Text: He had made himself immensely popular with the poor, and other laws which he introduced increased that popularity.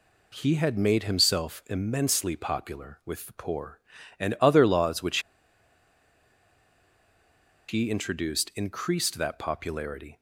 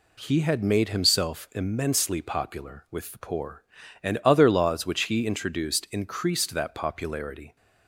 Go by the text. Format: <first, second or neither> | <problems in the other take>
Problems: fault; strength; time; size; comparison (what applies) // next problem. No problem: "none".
second | pauses between "which" and "he"; strong; at 5.1 s; 2.4 s long